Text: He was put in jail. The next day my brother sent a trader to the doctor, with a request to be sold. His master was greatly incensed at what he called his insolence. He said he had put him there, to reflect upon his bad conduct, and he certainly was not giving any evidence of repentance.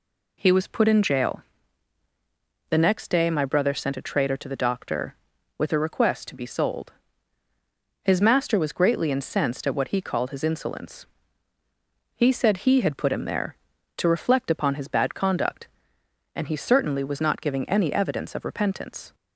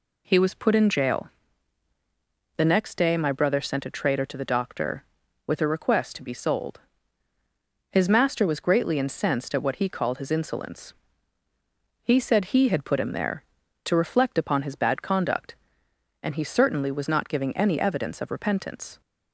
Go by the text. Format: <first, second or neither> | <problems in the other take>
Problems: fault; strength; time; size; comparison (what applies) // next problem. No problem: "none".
neither | none